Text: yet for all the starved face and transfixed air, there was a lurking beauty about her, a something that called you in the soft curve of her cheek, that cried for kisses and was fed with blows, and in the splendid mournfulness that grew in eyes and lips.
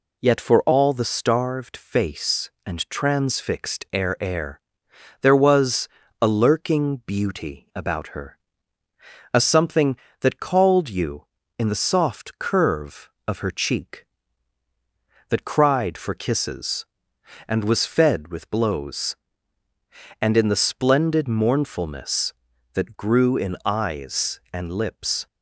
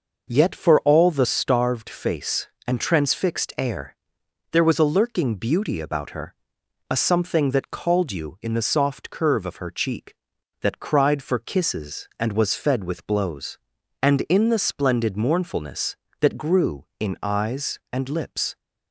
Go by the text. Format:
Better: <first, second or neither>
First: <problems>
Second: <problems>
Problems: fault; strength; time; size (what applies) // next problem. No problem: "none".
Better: second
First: says "air" twice; at 4.1 s // pauses between "was" and "a"; slight; at 5.8 s; 0.32 s long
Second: none